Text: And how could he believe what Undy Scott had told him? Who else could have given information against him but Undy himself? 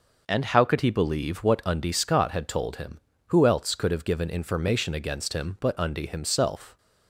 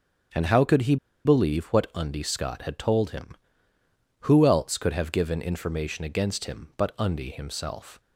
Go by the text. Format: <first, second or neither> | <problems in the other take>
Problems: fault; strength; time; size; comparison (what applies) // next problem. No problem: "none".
first | starts louder than the rest; until 1.6 s; 7 dB // pauses between "he" and "believe"; slight; at 0.9 s; 0.29 s long